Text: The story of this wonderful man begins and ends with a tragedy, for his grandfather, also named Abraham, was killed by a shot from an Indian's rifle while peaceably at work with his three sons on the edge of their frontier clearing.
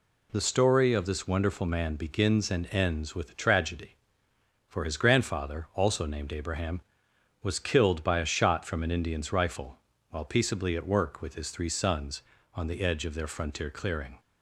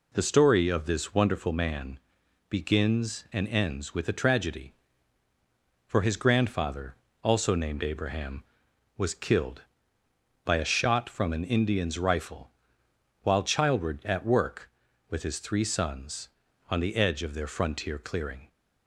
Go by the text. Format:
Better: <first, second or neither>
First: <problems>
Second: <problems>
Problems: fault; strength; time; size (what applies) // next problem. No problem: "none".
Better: first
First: pauses between "rifle" and "while"; slight; at 9.7 s; 0.32 s long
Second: pauses between "man" and "begins"; noticeable; at 1.9 s; 0.52 s long // pauses between "rifle" and "while"; noticeable; at 12.4 s; 0.72 s long // says "childward" for "peaceably"; at 13.4 s